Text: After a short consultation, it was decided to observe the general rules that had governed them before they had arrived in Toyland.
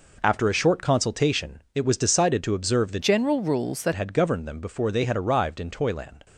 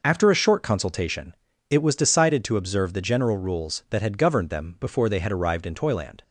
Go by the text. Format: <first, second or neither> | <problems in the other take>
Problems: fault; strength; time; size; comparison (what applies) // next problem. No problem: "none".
second | changes voice from "general" to "that"; from 3.0 to 3.9 s; 0.9 s long